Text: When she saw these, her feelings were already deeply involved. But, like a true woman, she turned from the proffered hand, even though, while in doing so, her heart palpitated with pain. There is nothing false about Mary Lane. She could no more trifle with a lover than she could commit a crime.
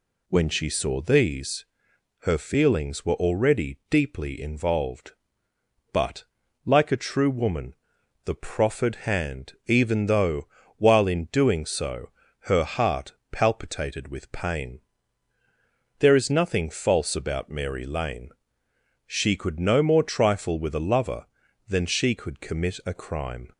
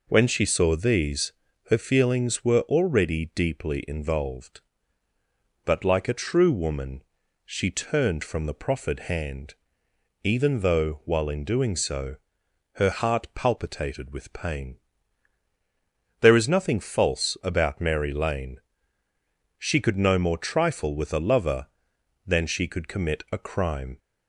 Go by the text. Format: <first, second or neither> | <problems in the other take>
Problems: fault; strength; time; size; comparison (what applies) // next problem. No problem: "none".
second | skips "she turned from"; at 7.9 s // pauses between "heart" and "palpitated"; slight; at 13.1 s; 0.18 s long